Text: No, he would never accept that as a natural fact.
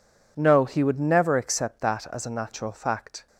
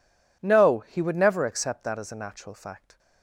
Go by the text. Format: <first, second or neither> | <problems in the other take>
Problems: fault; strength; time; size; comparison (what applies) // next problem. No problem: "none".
neither | none